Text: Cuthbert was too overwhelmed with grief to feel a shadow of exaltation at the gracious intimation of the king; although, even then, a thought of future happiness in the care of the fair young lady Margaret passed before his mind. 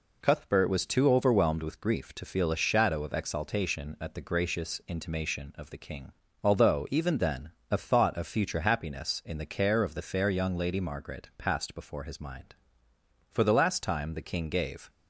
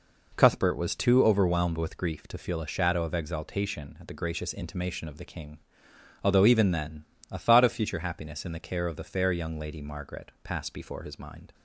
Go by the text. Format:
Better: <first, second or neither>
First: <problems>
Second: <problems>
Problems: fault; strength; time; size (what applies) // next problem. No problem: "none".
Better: second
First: goes on to say "For the last time the king gave"; from 13.2 s on; 1.6 s long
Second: none